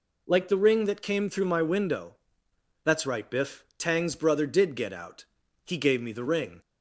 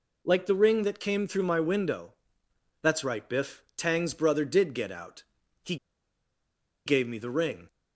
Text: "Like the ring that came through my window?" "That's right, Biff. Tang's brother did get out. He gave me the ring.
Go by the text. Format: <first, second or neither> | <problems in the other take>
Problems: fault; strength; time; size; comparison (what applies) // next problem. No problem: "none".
first | pauses between "He" and "gave"; at 5.7 s; 1.1 s long